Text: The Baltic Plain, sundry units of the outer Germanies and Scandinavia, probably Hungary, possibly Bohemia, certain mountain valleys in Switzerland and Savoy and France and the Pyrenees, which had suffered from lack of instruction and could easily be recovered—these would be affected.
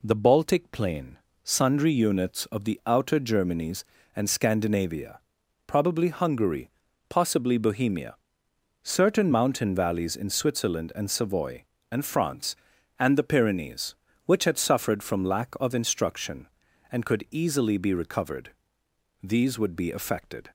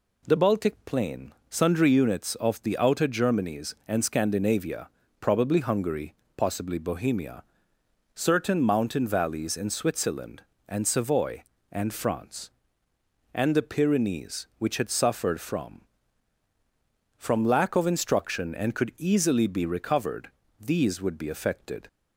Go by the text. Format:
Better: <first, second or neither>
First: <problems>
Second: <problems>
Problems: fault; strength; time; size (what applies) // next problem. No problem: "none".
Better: first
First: none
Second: says "from" twice; at 17.1 s